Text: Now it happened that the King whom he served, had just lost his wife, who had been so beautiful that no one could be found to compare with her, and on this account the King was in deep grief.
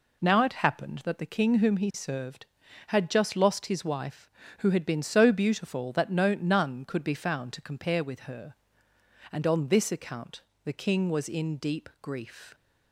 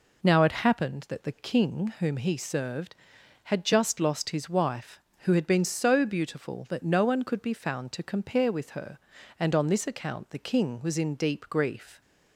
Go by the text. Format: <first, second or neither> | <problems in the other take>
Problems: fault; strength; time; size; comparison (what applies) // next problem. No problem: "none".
second | says "none" for "one"; at 6.3 s // pauses between "account" and "the"; slight; at 10.4 s; 0.22 s long